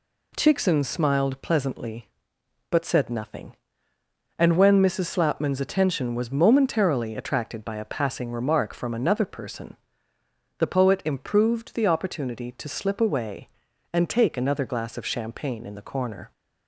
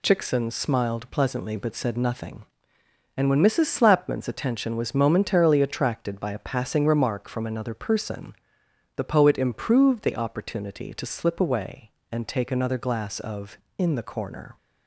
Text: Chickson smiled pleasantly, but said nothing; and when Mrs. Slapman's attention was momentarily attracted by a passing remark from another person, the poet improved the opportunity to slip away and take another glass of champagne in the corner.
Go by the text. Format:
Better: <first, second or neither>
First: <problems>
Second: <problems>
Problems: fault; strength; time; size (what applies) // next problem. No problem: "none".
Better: first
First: none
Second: skips "champagne"; at 13.6 s